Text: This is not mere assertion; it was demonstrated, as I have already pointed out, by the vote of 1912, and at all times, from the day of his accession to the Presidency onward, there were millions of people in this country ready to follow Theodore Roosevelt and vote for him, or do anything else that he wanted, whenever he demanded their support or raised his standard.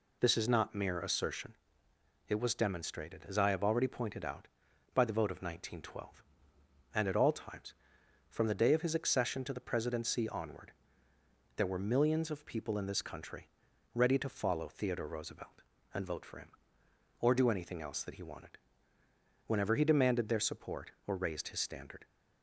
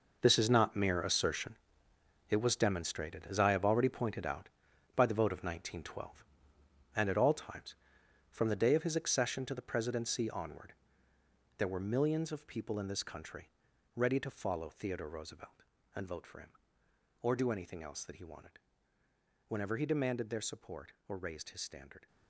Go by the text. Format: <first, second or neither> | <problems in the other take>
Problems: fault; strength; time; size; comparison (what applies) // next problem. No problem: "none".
first | gets quieter; strong; throughout; 12.5 dB // pauses between "country" and "ready"; at 13.5 s; 0.44 s long; also in the first